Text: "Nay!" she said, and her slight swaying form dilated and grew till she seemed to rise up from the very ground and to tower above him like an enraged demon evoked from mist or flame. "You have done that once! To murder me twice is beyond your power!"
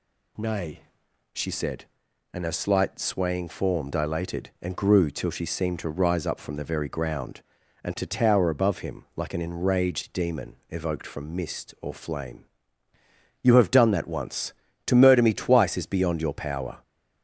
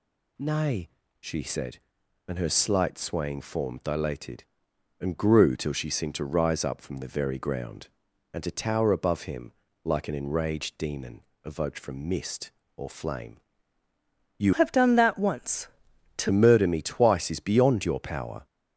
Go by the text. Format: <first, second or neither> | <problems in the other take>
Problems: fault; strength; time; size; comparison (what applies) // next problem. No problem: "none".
first | pauses between "him" and "like"; slight; at 9.5 s; 0.32 s long // pauses between "demon" and "evoked"; slight; at 11.2 s; 0.24 s long // changes voice from "have" to "To"; from 14.5 to 16.2 s; 1.7 s long